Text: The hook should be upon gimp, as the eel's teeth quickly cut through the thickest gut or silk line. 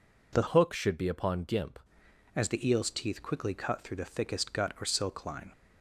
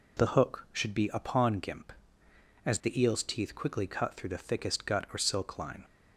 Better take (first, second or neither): second